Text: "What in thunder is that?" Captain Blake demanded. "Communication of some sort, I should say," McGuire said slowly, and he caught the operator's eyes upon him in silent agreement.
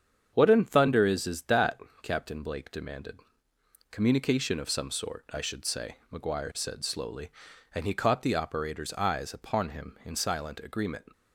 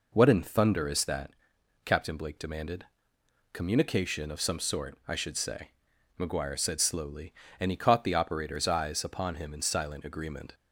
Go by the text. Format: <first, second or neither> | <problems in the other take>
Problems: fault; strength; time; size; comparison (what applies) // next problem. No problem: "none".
second | starts louder than the rest; strong; until 1.3 s; 7.5 dB // says "is" twice; at 1.2 s